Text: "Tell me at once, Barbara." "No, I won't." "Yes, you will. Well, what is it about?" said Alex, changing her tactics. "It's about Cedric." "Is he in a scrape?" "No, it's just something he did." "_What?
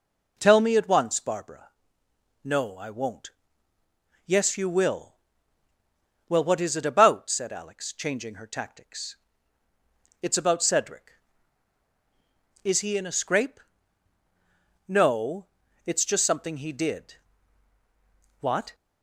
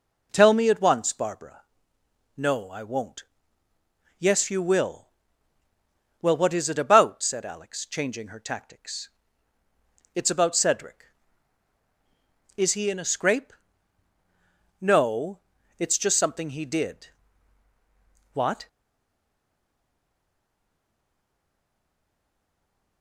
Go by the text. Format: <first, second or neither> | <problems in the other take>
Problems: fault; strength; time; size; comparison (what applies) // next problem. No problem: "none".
first | stays silent after the last word; strong; from 18.6 s on; 4.4 s long